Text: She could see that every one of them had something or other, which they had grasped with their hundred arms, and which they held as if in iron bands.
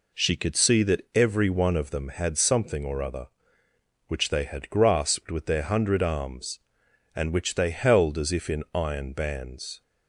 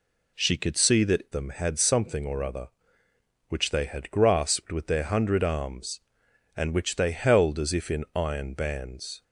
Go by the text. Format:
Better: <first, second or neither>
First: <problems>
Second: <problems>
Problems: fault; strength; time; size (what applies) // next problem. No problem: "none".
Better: first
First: none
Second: skips "every one of"; at 1.2 s